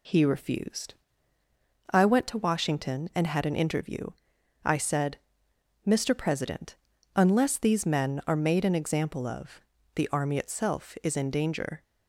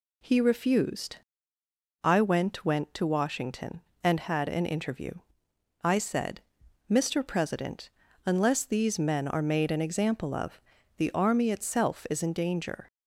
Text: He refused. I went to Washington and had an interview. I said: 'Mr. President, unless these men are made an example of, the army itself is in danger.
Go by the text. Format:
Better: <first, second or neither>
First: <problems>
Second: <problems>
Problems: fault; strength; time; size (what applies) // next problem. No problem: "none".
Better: first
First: none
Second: says "went" twice; at 2.6 s